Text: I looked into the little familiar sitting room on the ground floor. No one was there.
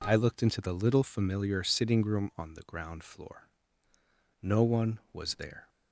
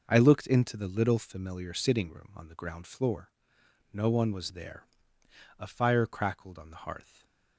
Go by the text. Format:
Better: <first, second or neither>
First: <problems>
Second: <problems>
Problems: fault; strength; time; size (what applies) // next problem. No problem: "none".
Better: first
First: none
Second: goes on to say "A fire crackled on the hearth"; from 5.5 s on; 1.6 s long // stays silent after the last word; slight; from 7.0 s on; 0.5 s long